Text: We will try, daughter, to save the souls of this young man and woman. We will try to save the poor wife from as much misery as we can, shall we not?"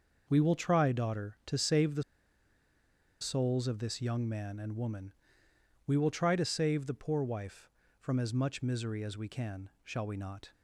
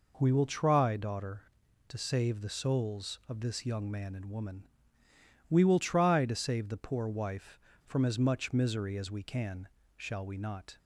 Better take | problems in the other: second | pauses between "the" and "souls"; at 2.0 s; 1.1 s long

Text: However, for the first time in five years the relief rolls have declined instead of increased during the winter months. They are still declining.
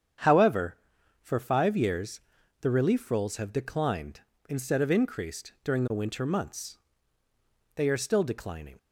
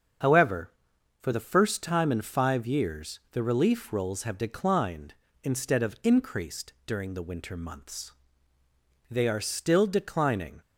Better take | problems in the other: second | starts louder than the rest; strong; until 1.7 s; 8 dB; also in the second // skips "the first time in"; at 1.3 s // pauses between "years" and "the"; at 2.1 s; 0.40 s long

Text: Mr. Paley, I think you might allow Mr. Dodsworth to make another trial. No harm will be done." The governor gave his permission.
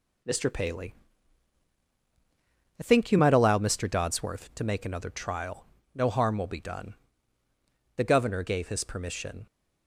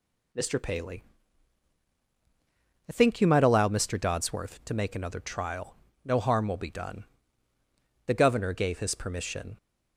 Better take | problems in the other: second | gets quieter; throughout; 6 dB

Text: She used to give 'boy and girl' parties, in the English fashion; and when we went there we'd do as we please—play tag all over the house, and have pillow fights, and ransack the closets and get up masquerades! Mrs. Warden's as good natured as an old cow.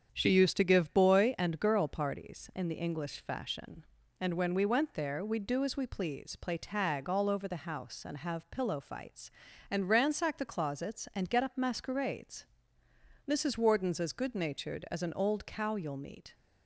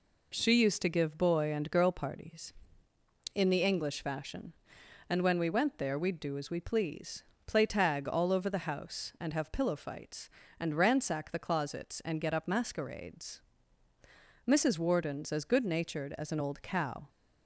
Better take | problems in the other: second | starts louder than the rest; strong; until 1.1 s; 7.5 dB // goes on to say "You'll meet"; from 15.7 s on; 0.58 s long

